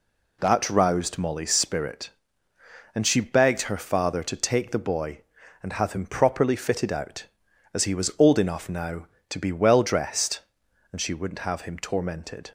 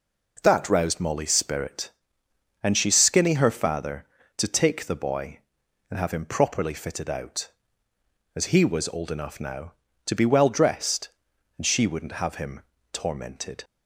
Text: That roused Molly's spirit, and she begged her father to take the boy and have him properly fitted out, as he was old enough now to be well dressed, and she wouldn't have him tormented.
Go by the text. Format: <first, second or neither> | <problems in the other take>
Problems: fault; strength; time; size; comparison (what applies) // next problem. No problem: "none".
first | says "skinny" for "begged"; at 2.9 s // pauses between "him" and "tormented"; slight; at 12.6 s; 0.30 s long